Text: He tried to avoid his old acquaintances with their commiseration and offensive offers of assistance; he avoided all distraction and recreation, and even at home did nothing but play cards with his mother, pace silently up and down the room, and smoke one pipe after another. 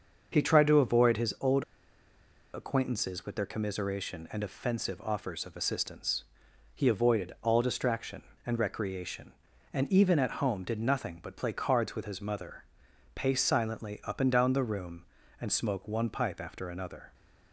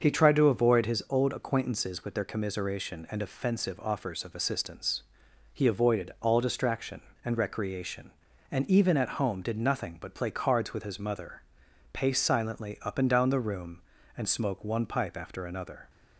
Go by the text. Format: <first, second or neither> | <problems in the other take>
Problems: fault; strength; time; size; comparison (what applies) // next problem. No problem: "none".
second | starts louder than the rest; until 1.3 s; 6.5 dB; also in the second // pauses between "old" and "acquaintances"; noticeable; at 1.6 s; 0.90 s long